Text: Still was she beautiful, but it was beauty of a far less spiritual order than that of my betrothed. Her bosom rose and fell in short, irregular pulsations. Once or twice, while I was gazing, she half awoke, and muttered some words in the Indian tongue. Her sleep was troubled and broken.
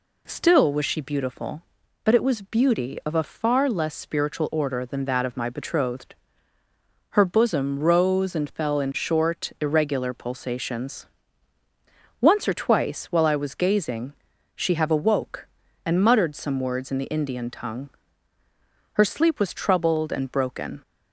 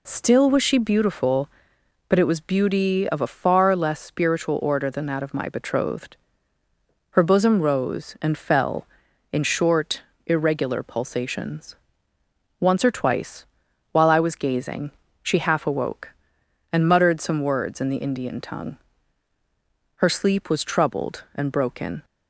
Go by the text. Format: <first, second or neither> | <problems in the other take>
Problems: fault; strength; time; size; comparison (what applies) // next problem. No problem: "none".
second | says "have" for "half"; at 14.7 s